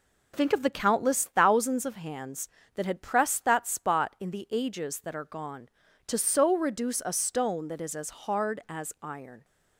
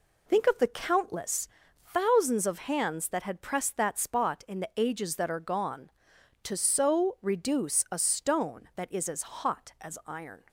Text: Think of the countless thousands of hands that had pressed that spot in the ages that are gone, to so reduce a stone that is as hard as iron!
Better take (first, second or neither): first